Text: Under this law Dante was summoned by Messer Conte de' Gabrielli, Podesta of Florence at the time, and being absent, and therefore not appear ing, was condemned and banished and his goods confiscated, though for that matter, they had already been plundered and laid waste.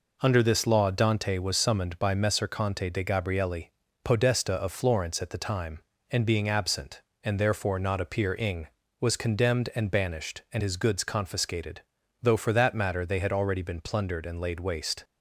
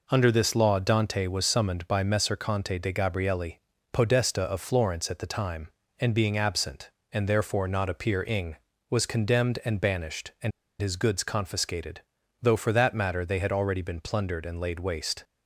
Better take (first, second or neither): first